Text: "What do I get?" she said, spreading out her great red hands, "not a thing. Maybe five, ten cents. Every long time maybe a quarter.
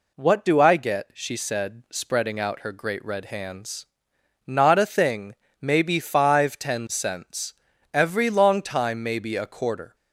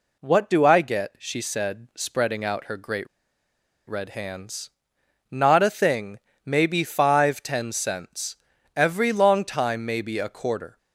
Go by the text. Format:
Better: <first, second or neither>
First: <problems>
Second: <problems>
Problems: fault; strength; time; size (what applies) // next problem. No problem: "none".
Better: first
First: none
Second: pauses between "great" and "red"; noticeable; at 3.0 s; 0.81 s long